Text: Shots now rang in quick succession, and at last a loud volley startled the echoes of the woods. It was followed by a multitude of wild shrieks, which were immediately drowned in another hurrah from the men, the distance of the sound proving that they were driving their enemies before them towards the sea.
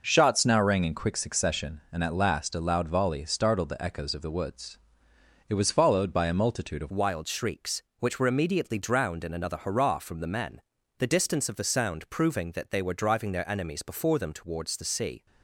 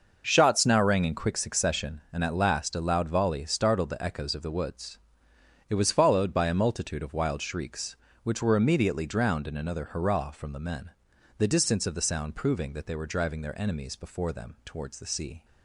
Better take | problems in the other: second | changes voice at "wild"; from 6.8 s on; 8.4 s long

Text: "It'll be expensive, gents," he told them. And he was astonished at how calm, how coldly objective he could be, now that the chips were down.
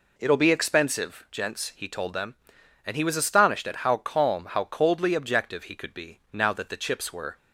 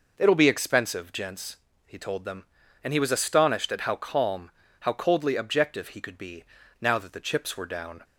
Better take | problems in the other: second | stops before "down"; at 7.3 s

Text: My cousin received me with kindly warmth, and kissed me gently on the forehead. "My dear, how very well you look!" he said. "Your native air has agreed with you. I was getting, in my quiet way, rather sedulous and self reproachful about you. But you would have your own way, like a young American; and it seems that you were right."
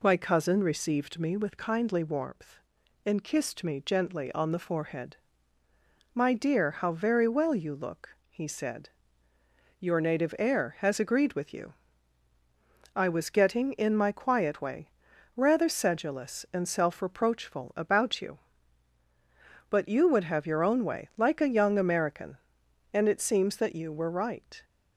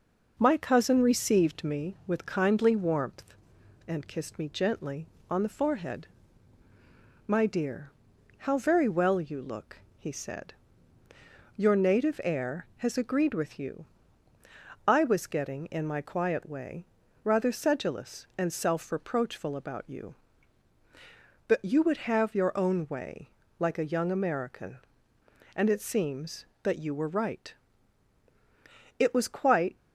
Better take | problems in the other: first | goes on to say "It was quite"; noticeable; from 28.9 s on; 0.76 s long

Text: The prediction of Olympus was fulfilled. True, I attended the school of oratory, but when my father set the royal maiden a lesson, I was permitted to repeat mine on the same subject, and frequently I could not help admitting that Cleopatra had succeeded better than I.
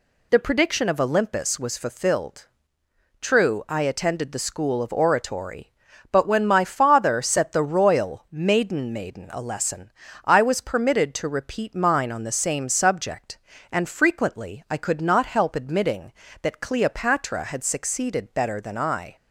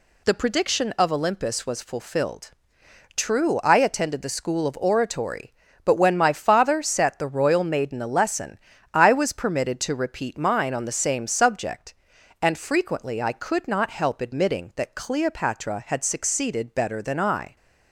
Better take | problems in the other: second | says "maiden" twice; at 8.9 s

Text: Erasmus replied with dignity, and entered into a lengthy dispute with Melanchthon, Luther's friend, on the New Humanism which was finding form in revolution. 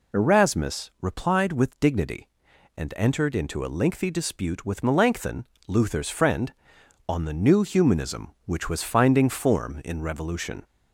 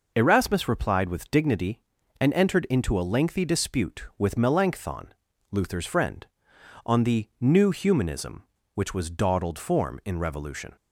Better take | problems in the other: first | says "dawdled" for "finding"; at 9.0 s

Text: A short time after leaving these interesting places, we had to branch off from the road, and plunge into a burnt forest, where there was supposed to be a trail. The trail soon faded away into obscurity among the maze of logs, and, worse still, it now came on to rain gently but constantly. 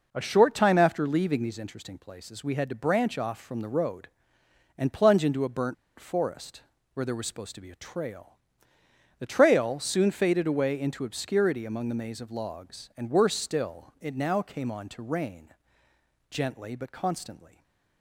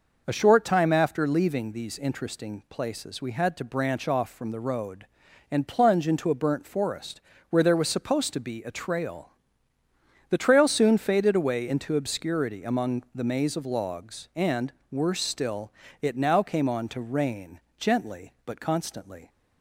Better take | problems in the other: second | pauses between "burnt" and "forest"; slight; at 5.7 s; 0.23 s long // pauses between "rain" and "gently"; noticeable; at 15.4 s; 0.80 s long; slight in the second // stays silent after the last word; slight; from 17.4 s on; 0.6 s long

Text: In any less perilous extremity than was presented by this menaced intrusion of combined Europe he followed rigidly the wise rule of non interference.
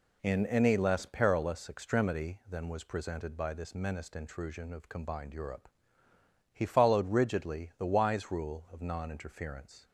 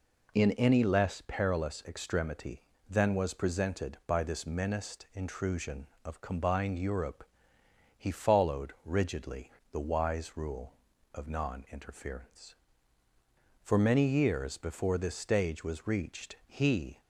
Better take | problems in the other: first | pauses between "Europe" and "he"; noticeable; at 7.2 s; 0.74 s long; noticeable in the first // pauses between "rigidly" and "the"; slight; at 9.4 s; 0.22 s long // goes on to say "For many years before this stage was reached he"; strong; from 13.6 s on; 3.3 s long

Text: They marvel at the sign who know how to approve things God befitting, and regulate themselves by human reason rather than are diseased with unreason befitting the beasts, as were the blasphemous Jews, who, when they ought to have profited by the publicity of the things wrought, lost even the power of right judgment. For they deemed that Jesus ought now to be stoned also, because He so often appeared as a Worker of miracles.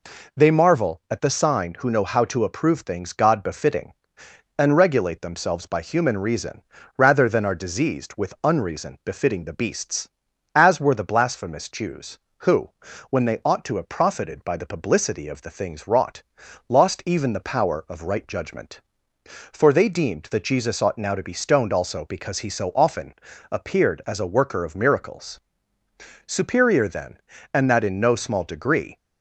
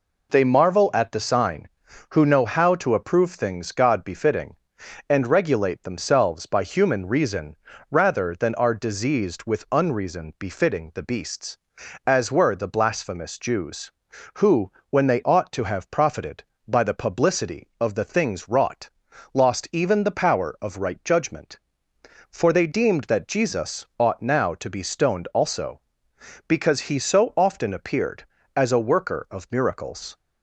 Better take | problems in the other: second | pauses between "reason" and "rather"; slight; at 6.6 s; 0.34 s long; slight in the second // pauses between "often" and "appeared"; slight; at 23.1 s; 0.36 s long // goes on to say "Superior then and that in no small degree"; strong; from 26.2 s on; 2.7 s long

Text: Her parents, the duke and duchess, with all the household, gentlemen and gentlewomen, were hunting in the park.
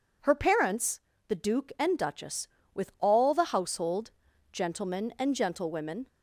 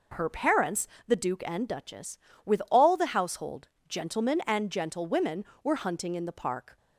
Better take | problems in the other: second | stops before "were hunting in the park"; at 6.0 s

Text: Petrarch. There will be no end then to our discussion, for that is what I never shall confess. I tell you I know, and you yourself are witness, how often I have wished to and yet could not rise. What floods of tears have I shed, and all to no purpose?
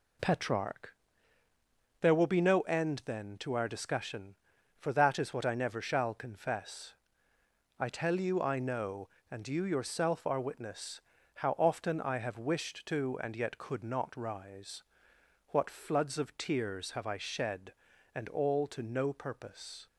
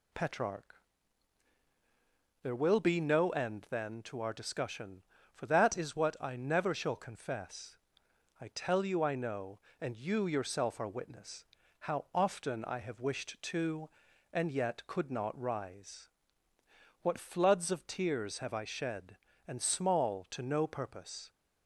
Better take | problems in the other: first | says "small" for "all"; at 19.6 s

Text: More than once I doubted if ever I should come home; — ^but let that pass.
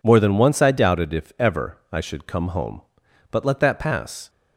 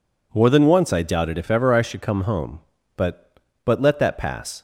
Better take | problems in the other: first | says "but" twice; at 3.6 s

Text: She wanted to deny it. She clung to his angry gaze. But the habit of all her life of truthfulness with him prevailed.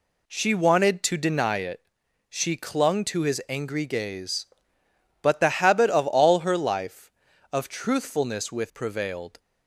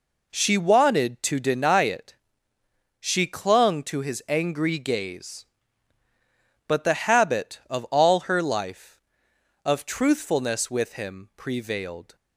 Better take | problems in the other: second | skips "him"; at 8.7 s

